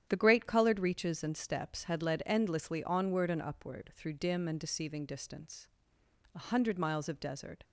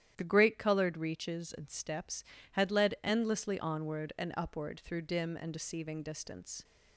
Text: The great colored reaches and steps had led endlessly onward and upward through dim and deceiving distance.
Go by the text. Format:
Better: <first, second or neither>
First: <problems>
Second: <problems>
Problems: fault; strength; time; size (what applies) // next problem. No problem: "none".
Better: second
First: starts louder than the rest; strong; until 1.1 s; 10 dB // goes on to say "A hundred miles of desert"; noticeable; from 6.3 s on; 1.2 s long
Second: starts louder than the rest; strong; until 1.1 s; 11 dB